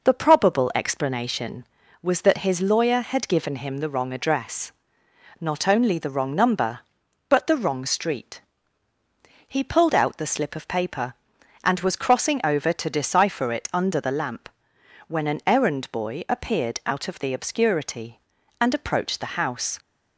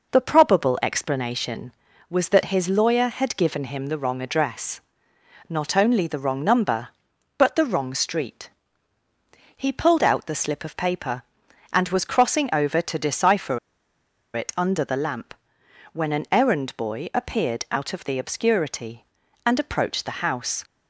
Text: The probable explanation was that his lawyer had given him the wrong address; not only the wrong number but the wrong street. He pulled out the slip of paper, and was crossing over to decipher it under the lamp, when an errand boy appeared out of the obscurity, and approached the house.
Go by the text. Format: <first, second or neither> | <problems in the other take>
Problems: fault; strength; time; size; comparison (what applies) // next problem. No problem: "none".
first | pauses between "decipher" and "it"; noticeable; at 13.5 s; 0.75 s long